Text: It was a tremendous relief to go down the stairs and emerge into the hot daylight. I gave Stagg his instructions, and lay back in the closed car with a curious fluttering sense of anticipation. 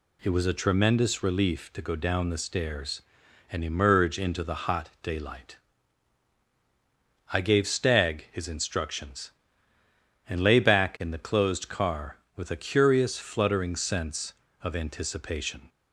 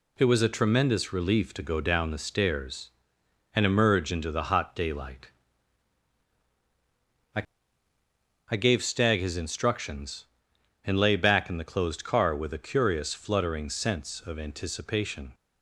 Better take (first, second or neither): first